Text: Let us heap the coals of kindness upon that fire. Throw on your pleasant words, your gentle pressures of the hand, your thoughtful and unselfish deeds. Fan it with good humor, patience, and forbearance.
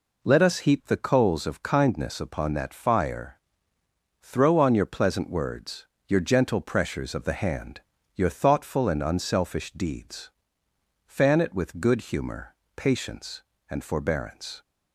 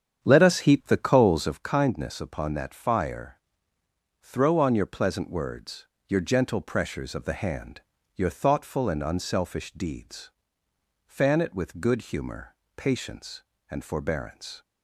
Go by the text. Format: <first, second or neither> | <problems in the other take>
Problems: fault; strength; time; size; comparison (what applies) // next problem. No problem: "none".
first | starts louder than the rest; strong; until 1.6 s; 8 dB